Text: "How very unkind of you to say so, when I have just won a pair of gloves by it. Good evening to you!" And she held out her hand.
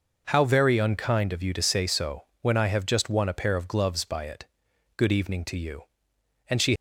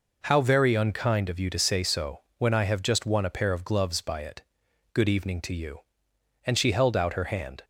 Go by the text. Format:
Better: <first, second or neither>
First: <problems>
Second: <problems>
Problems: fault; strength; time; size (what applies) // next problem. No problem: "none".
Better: second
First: stops before "held out her hand"; at 6.7 s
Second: none